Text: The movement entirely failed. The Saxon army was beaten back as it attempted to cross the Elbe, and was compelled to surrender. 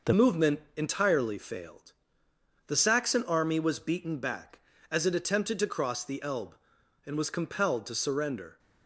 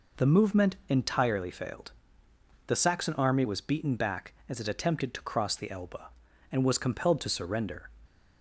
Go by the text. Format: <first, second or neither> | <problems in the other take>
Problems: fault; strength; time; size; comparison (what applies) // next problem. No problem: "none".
second | changes voice at "movement"; from 0.1 s on; 8.4 s long // pauses between "movement" and "entirely"; slight; at 0.6 s; 0.16 s long